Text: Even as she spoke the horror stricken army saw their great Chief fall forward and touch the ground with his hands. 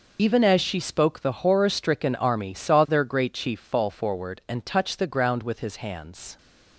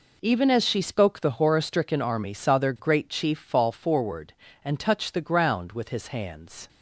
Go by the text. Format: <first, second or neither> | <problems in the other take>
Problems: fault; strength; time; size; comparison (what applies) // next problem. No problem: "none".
second | loses the start of "Even"; at 0.1 s; 60 ms